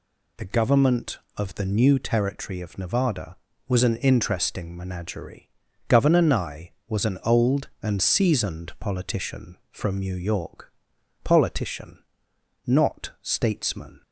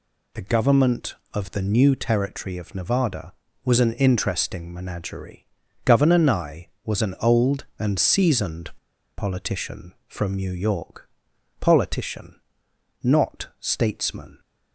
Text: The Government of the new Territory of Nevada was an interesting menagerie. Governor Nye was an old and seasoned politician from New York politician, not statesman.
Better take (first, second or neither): first